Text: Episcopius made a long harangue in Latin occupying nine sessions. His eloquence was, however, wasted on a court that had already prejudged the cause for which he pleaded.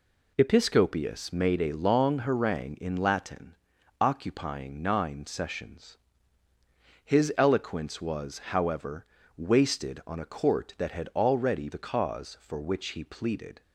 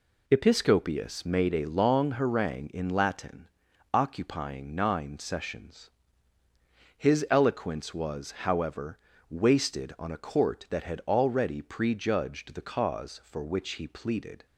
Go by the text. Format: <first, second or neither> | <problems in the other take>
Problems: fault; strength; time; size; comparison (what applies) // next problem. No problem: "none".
second | pauses between "Latin" and "occupying"; noticeable; at 3.5 s; 0.48 s long; noticeable in the second // skips "prejudged"; at 11.7 s